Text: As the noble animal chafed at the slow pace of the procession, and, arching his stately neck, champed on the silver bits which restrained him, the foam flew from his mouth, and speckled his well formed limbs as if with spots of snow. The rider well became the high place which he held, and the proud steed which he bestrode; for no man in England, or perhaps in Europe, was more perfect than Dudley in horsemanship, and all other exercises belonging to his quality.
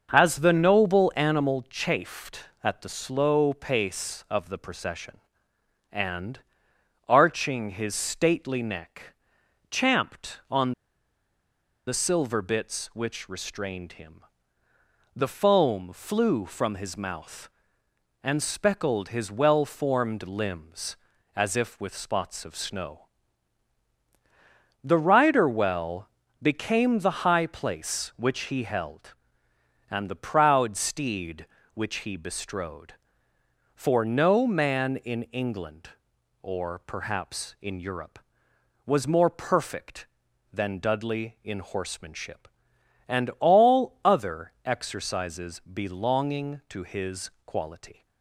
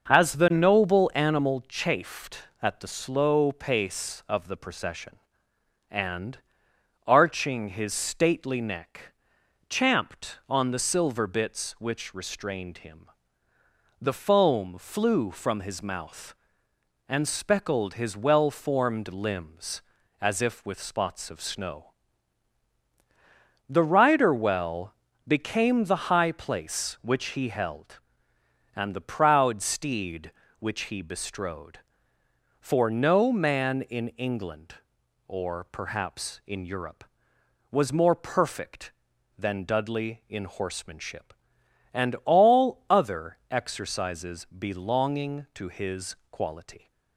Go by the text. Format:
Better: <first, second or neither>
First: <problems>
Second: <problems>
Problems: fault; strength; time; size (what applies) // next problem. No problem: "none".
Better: second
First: starts louder than the rest; until 1.1 s; 6.5 dB // pauses between "on" and "the"; at 10.7 s; 1.1 s long // pauses between "well" and "became"; slight; at 26.0 s; 0.32 s long // pauses between "his" and "quality"; slight; at 47.2 s; 0.16 s long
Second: starts louder than the rest; until 1.1 s; 6.5 dB // pauses between "well" and "became"; slight; at 24.9 s; 0.32 s long // pauses between "his" and "quality"; slight; at 46.1 s; 0.16 s long